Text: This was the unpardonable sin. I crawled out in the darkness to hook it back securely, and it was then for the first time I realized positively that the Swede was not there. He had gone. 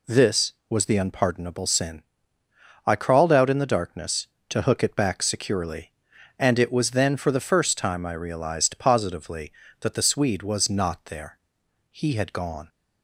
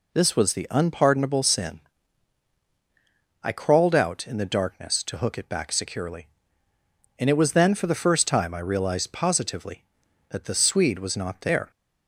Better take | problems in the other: first | stops before "He had gone"; at 11.7 s

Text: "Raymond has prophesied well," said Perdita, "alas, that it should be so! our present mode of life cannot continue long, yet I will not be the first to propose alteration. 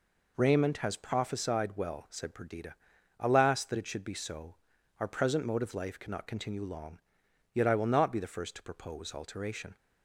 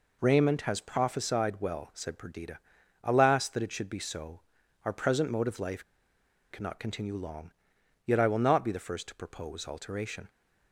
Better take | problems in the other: first | pauses between "life" and "cannot"; noticeable; at 5.8 s; 0.68 s long

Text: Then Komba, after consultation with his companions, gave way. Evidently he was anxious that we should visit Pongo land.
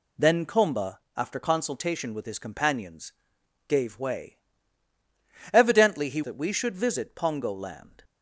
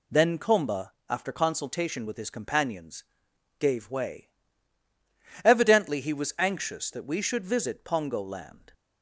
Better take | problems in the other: second | skips "was anxious"; at 6.2 s

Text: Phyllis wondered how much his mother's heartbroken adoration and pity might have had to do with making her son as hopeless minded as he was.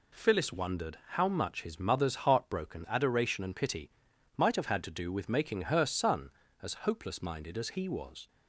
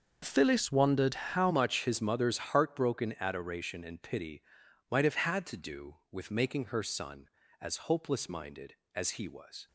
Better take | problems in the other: first | starts louder than the rest; until 1.2 s; 6 dB // changes voice at "much"; from 1.4 s on; 8.2 s long // pauses between "pity" and "might"; noticeable; at 4.4 s; 0.48 s long; noticeable in the first

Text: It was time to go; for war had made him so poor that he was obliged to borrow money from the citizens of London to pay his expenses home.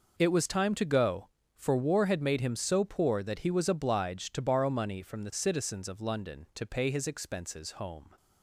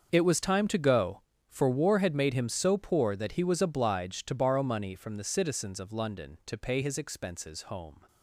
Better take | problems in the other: first | gets quieter; strong; throughout; 16 dB

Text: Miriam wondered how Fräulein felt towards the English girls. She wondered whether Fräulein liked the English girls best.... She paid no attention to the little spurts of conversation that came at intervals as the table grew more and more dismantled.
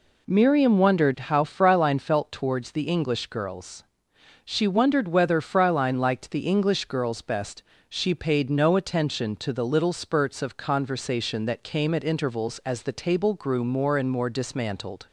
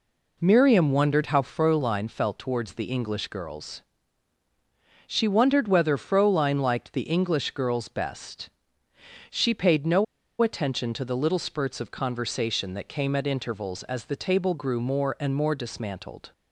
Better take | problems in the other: first | pauses between "no" and "attention"; at 10.0 s; 0.36 s long

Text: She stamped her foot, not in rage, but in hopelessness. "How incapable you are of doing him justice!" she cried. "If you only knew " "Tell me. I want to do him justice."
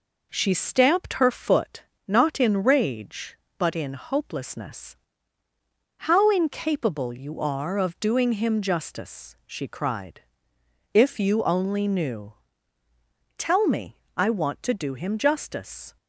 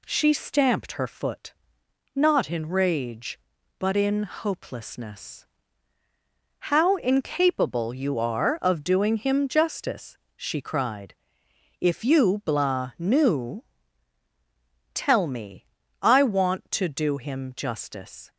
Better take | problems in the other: first | says "blah" for "only"; at 12.4 s

